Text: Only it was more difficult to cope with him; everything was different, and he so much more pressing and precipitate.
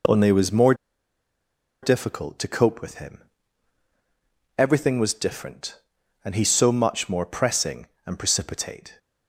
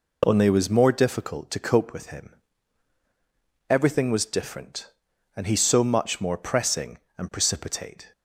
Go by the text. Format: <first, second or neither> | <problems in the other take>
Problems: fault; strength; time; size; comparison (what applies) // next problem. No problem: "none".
second | pauses between "more" and "difficult"; at 0.7 s; 1.0 s long